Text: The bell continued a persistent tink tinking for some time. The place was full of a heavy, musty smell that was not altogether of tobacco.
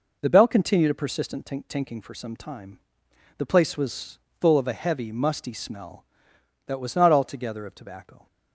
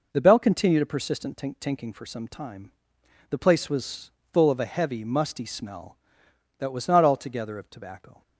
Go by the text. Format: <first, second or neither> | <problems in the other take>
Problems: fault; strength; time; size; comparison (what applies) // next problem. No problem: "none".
neither | pauses between "was" and "full"; slight; the same in both